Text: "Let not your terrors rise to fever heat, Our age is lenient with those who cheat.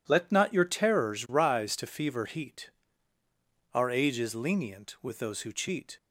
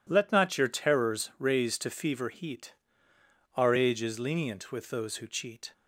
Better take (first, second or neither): first